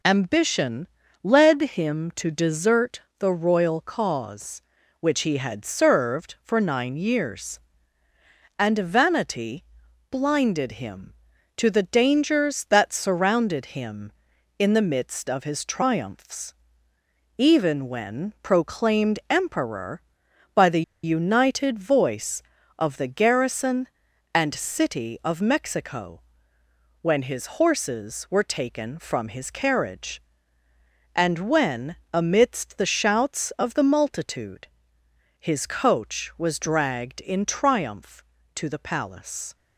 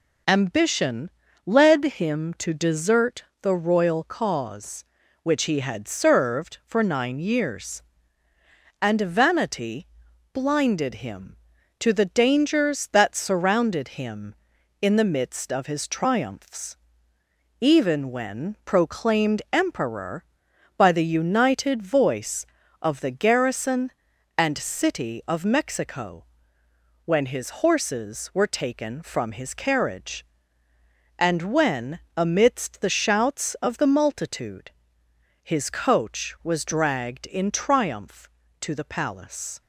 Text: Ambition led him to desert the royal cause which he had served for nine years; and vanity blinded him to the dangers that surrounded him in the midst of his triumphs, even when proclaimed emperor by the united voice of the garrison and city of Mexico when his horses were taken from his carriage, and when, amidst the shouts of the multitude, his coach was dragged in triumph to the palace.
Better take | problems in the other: second | pauses between "Ambition" and "led"; slight; at 0.8 s; 0.34 s long; slight in the second // pauses between "desert" and "the"; slight; at 3.0 s; 0.16 s long; slight in the second // pauses between "vanity" and "blinded"; noticeable; at 9.6 s; 0.46 s long; noticeable in the second // pauses between "the" and "united"; slight; at 20.8 s; 0.21 s long // pauses between "Mexico" and "when"; noticeable; at 26.2 s; 0.82 s long; noticeable in the second

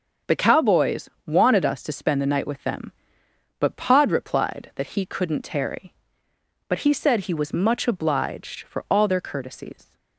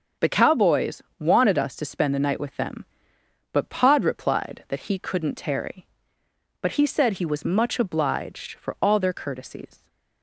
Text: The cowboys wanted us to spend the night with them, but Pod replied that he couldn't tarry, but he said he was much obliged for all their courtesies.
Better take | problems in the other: neither | starts louder than the rest; the same in both // pauses between "cowboys" and "wanted"; slight; the same in both

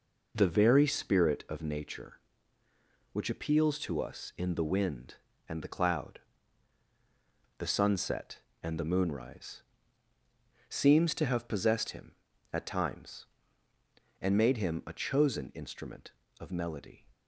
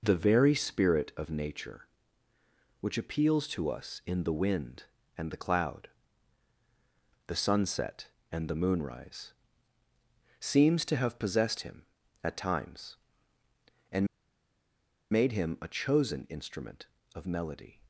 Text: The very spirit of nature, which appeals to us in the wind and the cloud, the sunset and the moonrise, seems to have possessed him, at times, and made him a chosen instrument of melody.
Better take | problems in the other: first | pauses between "and" and "made"; at 14.0 s; 1.0 s long

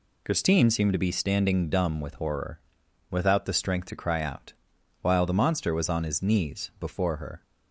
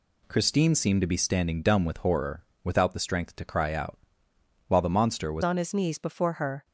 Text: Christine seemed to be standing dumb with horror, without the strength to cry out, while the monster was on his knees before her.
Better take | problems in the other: first | changes voice at "on"; from 5.4 s on; 1.2 s long

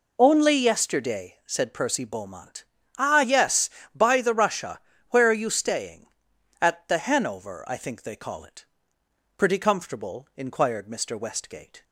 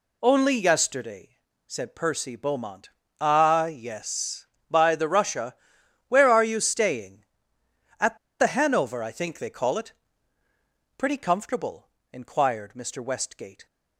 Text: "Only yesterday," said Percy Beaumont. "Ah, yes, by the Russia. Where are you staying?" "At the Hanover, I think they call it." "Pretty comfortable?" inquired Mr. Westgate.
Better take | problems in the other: first | pauses between "At" and "the"; slight; at 8.1 s; 0.22 s long

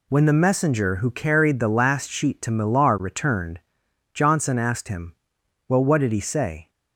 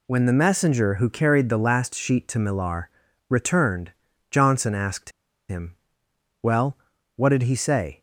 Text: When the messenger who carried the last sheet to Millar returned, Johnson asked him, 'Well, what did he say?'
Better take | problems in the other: first | pauses between "Millar" and "returned"; at 2.8 s; 0.40 s long // pauses between "asked" and "him"; at 5.1 s; 0.38 s long

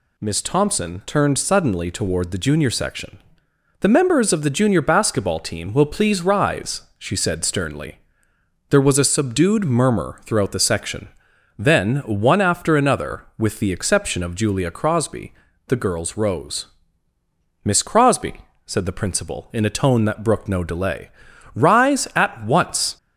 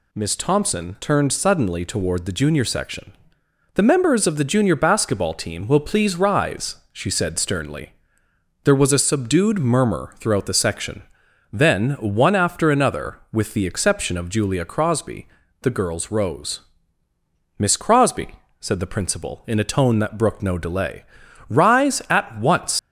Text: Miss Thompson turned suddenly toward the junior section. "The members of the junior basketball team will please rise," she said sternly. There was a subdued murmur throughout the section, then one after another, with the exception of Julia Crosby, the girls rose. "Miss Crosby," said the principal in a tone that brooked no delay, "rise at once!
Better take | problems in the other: first | leaves "once" unfinished; at 22.7 s; 120 ms

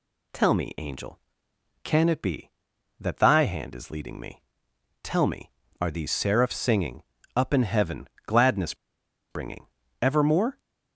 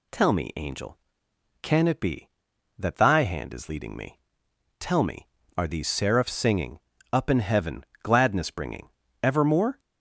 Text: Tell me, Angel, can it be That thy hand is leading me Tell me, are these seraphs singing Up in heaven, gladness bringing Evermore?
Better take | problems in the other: second | pauses between "me" and "Tell"; noticeable; at 4.4 s; 0.60 s long; noticeable in the second // pauses between "singing" and "Up"; slight; at 7.0 s; 0.34 s long; slight in the second // pauses between "gladness" and "bringing"; noticeable; at 8.7 s; 0.57 s long // pauses between "bringing" and "Evermore"; slight; at 9.6 s; 0.36 s long; slight in the second

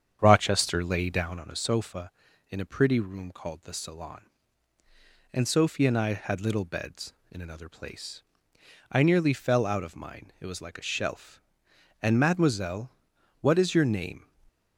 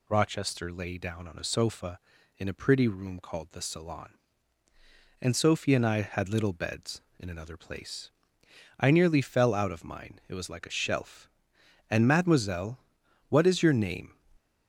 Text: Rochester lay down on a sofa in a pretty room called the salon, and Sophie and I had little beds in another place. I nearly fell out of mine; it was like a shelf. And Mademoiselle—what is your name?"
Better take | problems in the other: second | starts louder than the rest; strong; until 1.6 s; 8 dB // stays silent after the last word; slight; from 14.2 s on; 0.5 s long

